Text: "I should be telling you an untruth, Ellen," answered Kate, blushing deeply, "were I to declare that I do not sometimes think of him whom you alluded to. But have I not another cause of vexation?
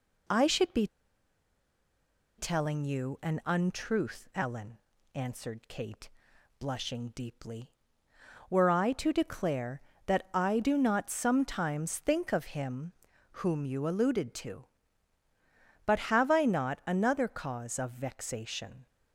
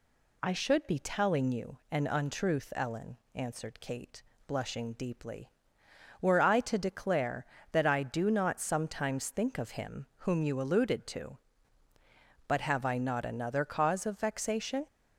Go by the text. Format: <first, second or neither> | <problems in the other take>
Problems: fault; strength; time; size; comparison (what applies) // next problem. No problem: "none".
second | pauses between "be" and "telling"; strong; at 0.8 s; 1.5 s long // pauses between "him" and "whom"; noticeable; at 12.9 s; 0.48 s long